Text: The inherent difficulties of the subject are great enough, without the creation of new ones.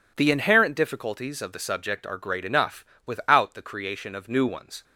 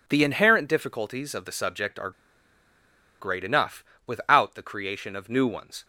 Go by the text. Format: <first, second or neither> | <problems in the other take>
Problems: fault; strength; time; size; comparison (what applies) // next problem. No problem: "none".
first | pauses between "are" and "great"; at 2.1 s; 1.0 s long